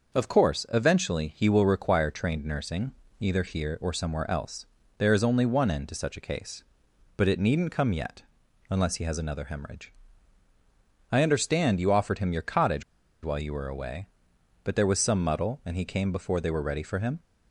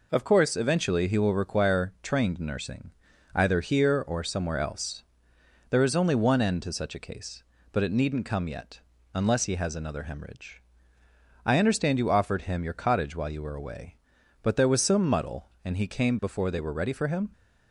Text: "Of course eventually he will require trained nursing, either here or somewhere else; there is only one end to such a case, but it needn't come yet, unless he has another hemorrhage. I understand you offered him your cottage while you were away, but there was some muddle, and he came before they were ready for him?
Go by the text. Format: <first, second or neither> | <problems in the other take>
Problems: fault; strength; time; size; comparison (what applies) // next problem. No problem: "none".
second | starts louder than the rest; until 1.2 s; 6 dB // pauses between "cottage" and "while"; at 12.8 s; 0.42 s long